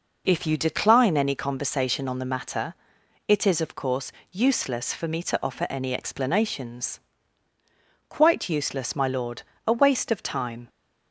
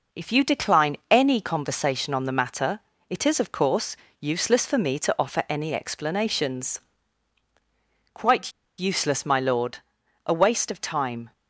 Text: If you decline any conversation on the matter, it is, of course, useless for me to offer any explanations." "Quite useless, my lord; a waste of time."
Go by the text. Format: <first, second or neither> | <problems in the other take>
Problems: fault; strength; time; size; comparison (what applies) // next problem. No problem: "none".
first | pauses between "Quite" and "useless"; slight; at 8.5 s; 0.26 s long